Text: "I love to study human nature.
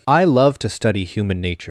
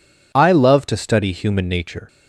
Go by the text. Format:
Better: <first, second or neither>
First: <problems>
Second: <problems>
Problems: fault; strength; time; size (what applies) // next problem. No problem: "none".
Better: second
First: leaves "nature" unfinished; at 1.6 s; 95 ms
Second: none